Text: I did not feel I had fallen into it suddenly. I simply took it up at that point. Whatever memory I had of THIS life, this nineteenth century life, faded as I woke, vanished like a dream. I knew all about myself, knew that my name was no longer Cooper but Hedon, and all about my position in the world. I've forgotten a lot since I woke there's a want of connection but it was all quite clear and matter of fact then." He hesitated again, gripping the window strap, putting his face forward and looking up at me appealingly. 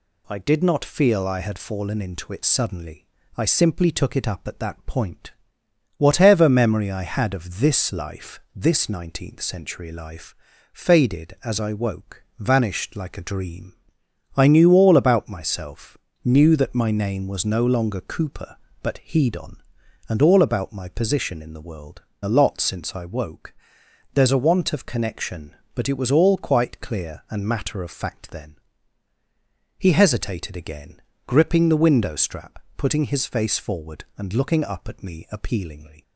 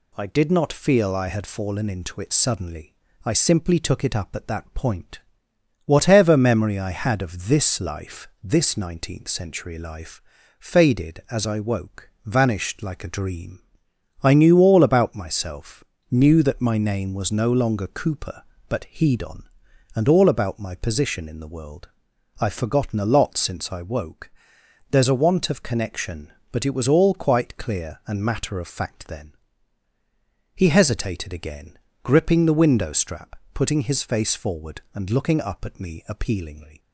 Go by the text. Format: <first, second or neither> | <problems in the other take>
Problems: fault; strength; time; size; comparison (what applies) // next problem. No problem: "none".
second | skips "I've forgotten"; at 22.1 s // pauses between "woke" and "there's"; noticeable; at 23.5 s; 0.60 s long; noticeable in the second